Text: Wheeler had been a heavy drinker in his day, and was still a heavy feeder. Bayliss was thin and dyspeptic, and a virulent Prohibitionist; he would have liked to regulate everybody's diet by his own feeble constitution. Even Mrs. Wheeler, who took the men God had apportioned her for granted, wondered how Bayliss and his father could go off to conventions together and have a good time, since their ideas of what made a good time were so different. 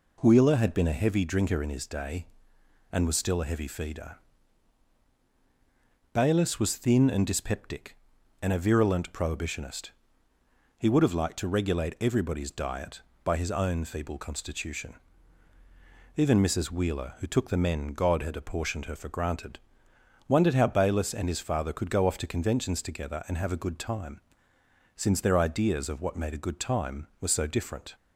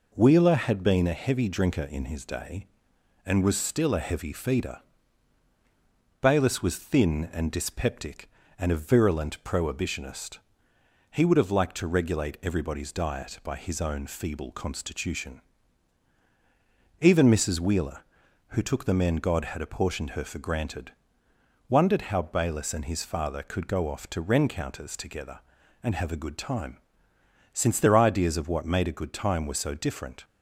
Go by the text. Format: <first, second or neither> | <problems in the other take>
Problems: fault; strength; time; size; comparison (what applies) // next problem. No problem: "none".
first | says "rencounters" for "conventions"; at 24.1 s